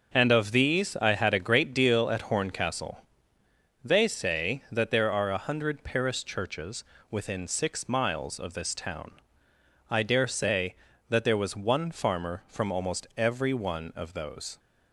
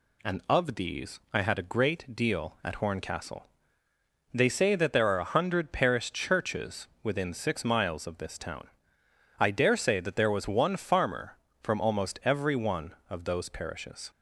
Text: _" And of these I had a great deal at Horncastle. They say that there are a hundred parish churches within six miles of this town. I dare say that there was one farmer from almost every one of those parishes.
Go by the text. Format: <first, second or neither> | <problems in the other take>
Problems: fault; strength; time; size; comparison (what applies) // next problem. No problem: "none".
second | starts louder than the rest; until 1.1 s; 6.5 dB // pauses between "churches" and "within"; slight; at 6.8 s; 0.26 s long // stops before "parishes"; at 14.5 s